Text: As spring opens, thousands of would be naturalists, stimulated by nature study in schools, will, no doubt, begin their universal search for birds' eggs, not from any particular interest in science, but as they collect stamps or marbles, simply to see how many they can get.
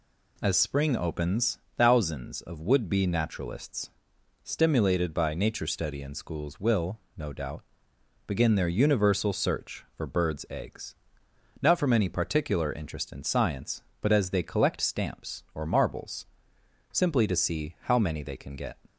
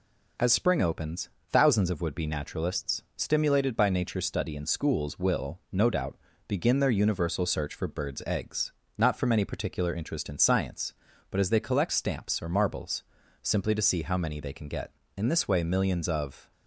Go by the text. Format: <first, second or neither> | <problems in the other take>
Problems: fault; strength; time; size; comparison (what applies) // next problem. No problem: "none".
first | goes on to say "In this way millions of"; from 15.1 s on; 1.3 s long